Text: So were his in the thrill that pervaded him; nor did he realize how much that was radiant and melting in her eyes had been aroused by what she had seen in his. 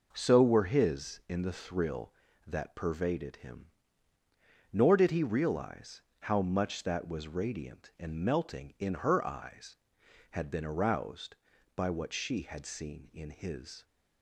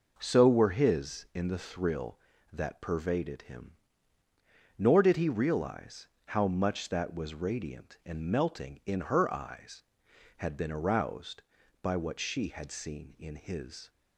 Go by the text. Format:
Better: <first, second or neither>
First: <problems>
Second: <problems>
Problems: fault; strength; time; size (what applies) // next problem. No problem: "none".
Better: neither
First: pauses between "realize" and "how"; slight; at 6.0 s; 0.18 s long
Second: pauses between "realize" and "how"; slight; at 6.0 s; 0.18 s long